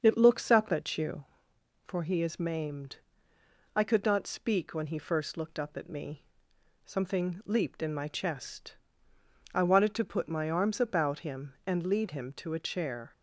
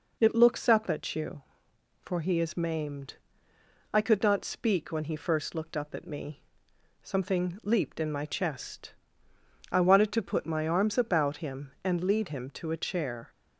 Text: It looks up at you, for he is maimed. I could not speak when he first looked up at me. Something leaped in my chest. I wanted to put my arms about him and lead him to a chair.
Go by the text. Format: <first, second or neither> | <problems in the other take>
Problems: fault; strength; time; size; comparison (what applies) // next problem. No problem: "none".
second | starts louder than the rest; until 1.5 s; 7 dB